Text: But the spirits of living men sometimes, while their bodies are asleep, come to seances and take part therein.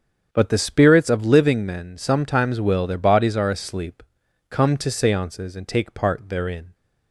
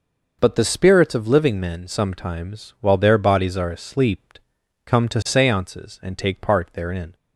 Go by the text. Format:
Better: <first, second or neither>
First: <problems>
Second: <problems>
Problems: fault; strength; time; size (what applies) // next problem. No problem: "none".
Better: second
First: starts louder than the rest; strong; until 1.3 s; 7.5 dB // says "will" for "while"; at 2.6 s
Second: none